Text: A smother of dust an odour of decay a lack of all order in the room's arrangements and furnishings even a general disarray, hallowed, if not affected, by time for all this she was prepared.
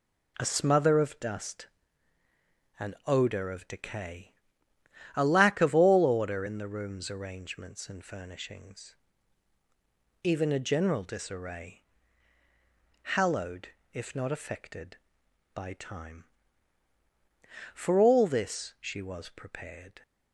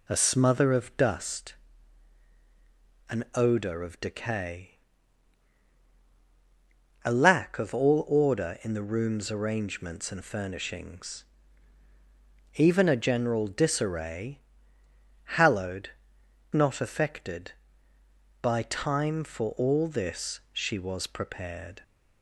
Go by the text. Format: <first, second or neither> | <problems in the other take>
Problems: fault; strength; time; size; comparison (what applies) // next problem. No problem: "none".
first | pauses between "dust" and "an"; strong; at 1.5 s; 1.5 s long; also in the first // pauses between "decay" and "a"; strong; at 4.7 s; 2.3 s long; noticeable in the first // pauses between "furnishings" and "even"; strong; at 11.2 s; 1.3 s long; strong in the first // skips "if"; at 16.2 s